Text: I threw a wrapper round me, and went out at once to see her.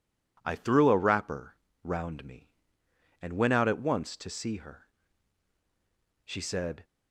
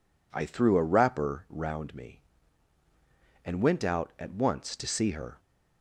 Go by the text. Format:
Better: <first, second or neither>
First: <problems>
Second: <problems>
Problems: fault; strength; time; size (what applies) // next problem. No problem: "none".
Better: second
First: pauses between "wrapper" and "round"; slight; at 1.5 s; 0.26 s long // goes on to say "She said"; from 6.2 s on; 0.60 s long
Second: none